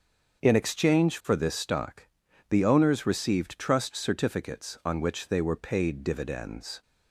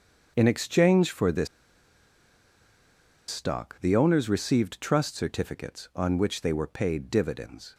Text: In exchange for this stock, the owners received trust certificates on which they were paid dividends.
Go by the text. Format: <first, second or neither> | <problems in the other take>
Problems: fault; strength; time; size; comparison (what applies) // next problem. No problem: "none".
first | starts louder than the rest; until 1.3 s; 7 dB; also in the first // pauses between "this" and "stock"; strong; at 1.4 s; 1.8 s long